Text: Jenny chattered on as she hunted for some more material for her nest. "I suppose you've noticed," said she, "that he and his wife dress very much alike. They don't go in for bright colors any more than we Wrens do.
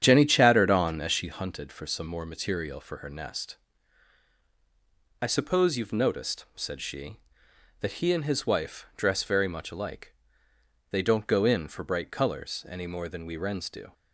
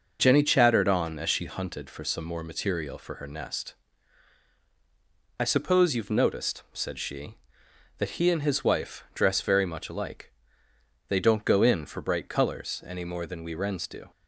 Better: second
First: starts louder than the rest; strong; until 1.2 s; 9 dB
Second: none

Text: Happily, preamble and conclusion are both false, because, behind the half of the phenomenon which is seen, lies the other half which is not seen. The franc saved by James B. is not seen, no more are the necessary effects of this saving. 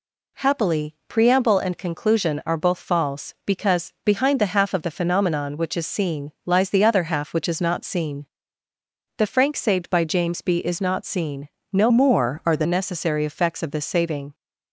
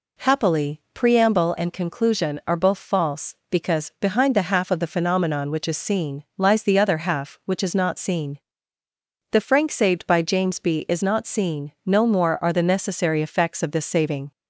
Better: second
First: changes voice from "more" to "the"; from 11.8 to 12.6 s; 0.8 s long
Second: none

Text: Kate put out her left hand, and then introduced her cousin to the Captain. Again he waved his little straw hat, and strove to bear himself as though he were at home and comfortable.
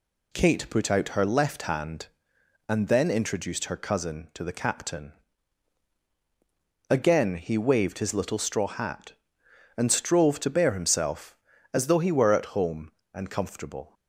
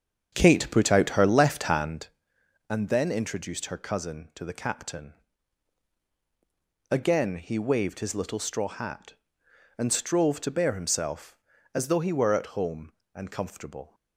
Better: first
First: none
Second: starts louder than the rest; strong; until 2.1 s; 7.5 dB

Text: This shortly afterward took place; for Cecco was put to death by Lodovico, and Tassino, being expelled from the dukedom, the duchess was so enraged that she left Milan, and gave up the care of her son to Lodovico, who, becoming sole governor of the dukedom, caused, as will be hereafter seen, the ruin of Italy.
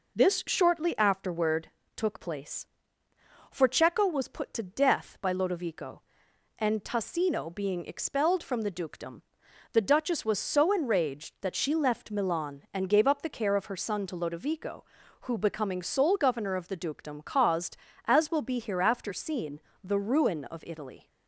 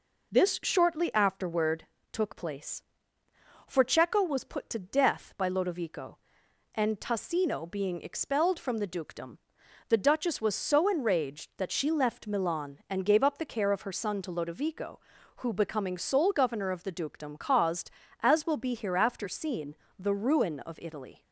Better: neither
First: pauses between "afterward" and "took"; slight; at 1.6 s; 0.26 s long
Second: pauses between "afterward" and "took"; slight; at 1.8 s; 0.26 s long

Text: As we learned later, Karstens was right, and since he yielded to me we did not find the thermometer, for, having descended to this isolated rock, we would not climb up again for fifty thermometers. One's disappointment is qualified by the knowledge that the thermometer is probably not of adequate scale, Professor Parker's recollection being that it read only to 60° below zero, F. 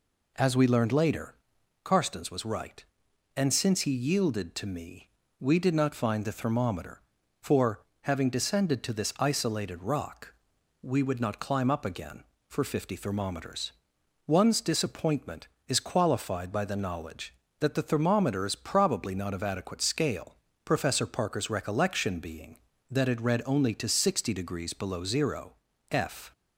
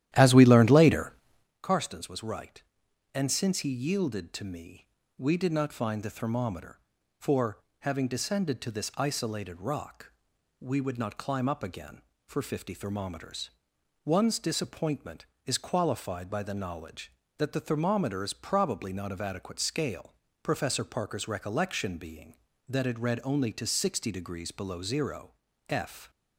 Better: first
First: pauses between "me" and "we"; slight; at 5.0 s; 0.32 s long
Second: starts louder than the rest; strong; until 1.5 s; 12.5 dB // pauses between "me" and "we"; slight; at 4.8 s; 0.32 s long

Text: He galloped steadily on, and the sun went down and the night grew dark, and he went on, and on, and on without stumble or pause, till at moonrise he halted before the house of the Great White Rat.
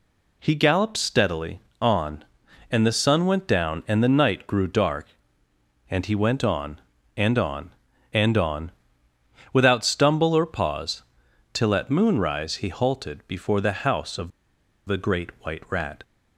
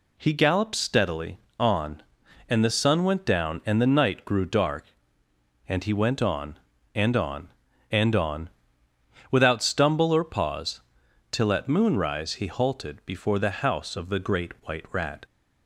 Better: second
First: pauses between "on" and "without"; noticeable; at 8.7 s; 0.82 s long // pauses between "of" and "the"; noticeable; at 14.3 s; 0.56 s long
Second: pauses between "on" and "without"; noticeable; at 8.4 s; 0.82 s long

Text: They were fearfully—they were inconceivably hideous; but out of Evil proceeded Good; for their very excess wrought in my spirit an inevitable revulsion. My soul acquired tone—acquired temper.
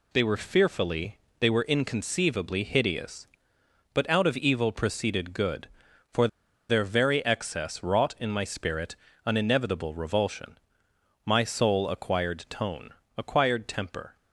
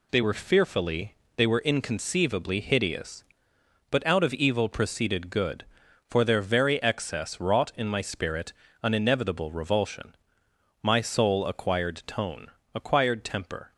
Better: second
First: pauses between "for" and "their"; at 6.2 s; 0.42 s long // pauses between "spirit" and "an"; slight; at 8.9 s; 0.28 s long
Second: pauses between "spirit" and "an"; slight; at 8.5 s; 0.28 s long

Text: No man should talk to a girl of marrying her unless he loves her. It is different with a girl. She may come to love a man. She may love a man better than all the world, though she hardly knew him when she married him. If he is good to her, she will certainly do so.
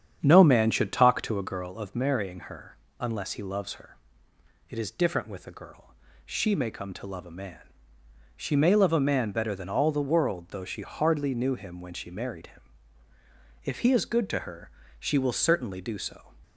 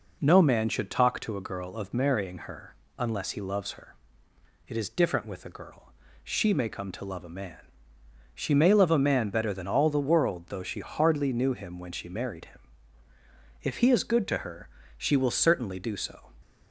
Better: second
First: starts louder than the rest; strong; until 1.7 s; 8.5 dB // pauses between "her" and "unless"; slight; at 2.7 s; 0.22 s long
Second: pauses between "her" and "unless"; slight; at 2.7 s; 0.22 s long

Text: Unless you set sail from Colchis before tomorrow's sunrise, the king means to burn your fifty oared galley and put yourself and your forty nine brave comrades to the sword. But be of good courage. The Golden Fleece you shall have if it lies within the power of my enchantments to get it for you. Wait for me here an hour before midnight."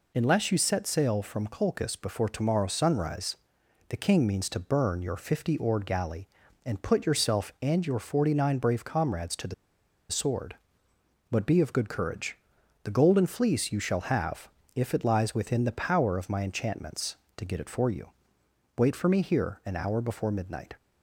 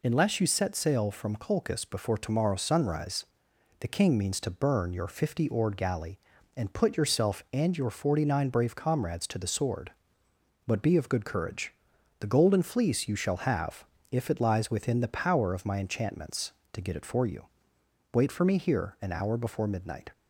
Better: second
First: pauses between "the" and "sword"; noticeable; at 9.5 s; 0.57 s long // pauses between "have" and "if"; slight; at 14.4 s; 0.28 s long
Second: pauses between "have" and "if"; slight; at 13.8 s; 0.28 s long

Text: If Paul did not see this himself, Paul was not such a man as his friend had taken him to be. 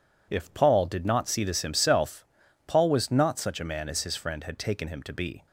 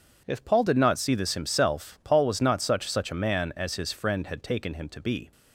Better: first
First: none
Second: says "such" twice; at 2.8 s

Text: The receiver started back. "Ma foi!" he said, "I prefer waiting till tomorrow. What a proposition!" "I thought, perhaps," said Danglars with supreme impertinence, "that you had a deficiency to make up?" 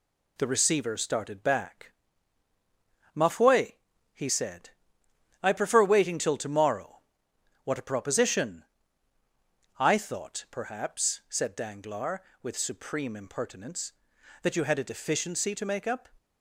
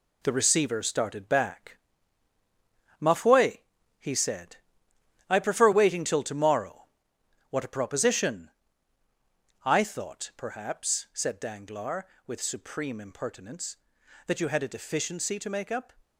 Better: first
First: none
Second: gets quieter; noticeable; throughout; 5.5 dB

